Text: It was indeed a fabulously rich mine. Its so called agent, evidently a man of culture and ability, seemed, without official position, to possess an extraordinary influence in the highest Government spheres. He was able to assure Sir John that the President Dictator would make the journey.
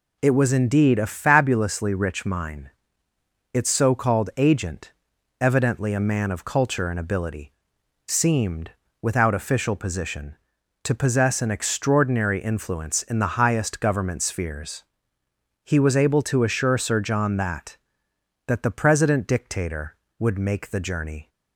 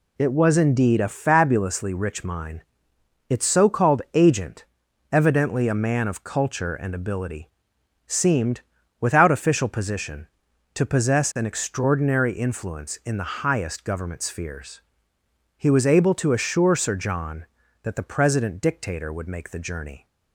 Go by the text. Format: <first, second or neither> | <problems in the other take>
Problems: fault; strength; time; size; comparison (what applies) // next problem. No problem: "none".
second | says "that" twice; at 18.4 s